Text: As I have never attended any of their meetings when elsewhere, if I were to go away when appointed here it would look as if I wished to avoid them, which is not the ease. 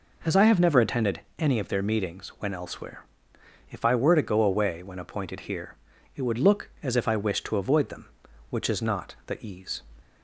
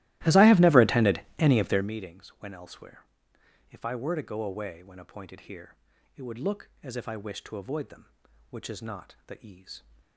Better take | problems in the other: first | starts louder than the rest; strong; until 1.9 s; 16.5 dB // pauses between "attended" and "any"; slight; at 1.2 s; 0.18 s long; slight in the first // pauses between "here" and "it"; at 5.7 s; 0.42 s long; also in the first

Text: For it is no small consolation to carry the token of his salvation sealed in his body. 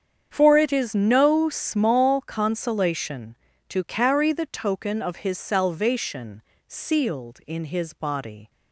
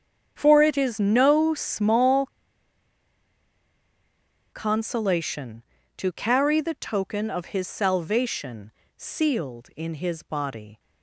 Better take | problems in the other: first | starts louder than the rest; strong; until 1.3 s; 8 dB; strong in the first // pauses between "small" and "consolation"; strong; at 2.2 s; 2.2 s long // pauses between "salvation" and "sealed"; slight; at 8.7 s; 0.26 s long; slight in the first

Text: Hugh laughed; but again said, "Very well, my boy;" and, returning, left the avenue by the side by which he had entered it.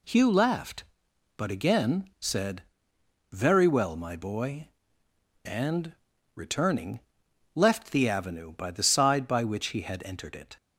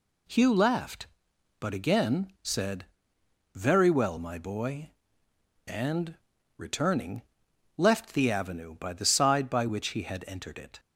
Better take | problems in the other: neither | none

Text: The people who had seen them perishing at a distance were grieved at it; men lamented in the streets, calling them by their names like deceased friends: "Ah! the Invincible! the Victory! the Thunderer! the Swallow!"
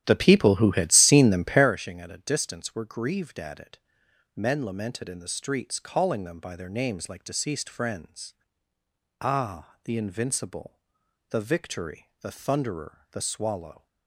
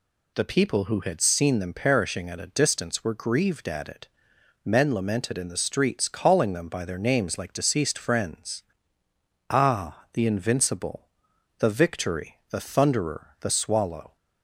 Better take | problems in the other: second | starts louder than the rest; strong; until 1.7 s; 11.5 dB

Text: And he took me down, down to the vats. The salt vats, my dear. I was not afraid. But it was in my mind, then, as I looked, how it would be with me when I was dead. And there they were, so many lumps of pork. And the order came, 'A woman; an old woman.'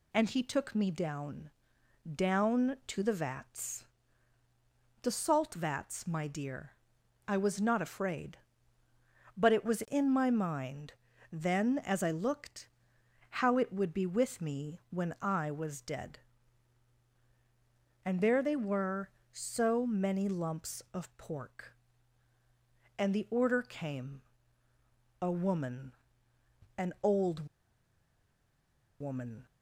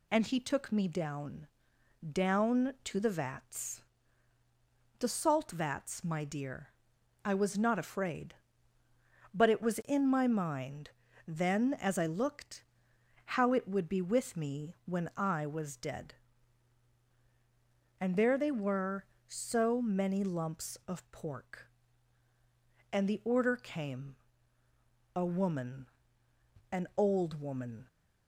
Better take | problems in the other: second | pauses between "old" and "woman"; strong; at 27.4 s; 1.5 s long

